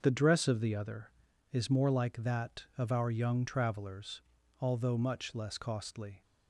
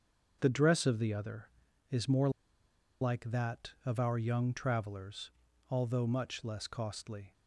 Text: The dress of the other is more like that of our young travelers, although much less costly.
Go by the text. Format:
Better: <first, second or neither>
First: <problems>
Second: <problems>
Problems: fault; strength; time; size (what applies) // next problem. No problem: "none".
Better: first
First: starts louder than the rest; until 1.0 s; 6.5 dB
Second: starts louder than the rest; until 1.4 s; 6.5 dB // pauses between "more" and "like"; noticeable; at 2.2 s; 0.71 s long